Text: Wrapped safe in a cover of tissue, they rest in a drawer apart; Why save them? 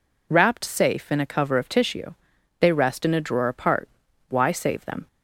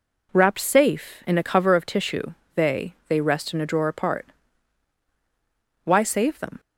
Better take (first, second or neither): first